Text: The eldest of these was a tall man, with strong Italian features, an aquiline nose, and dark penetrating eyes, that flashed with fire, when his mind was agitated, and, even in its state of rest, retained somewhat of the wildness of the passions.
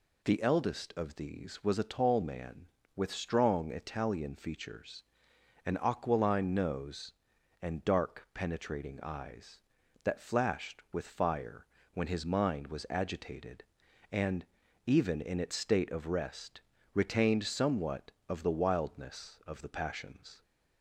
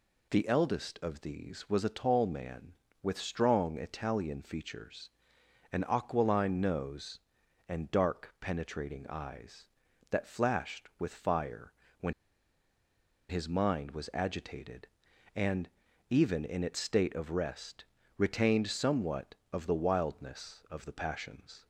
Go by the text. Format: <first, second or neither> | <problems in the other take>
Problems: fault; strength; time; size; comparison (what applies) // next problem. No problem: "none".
first | pauses between "when" and "his"; at 12.1 s; 1.1 s long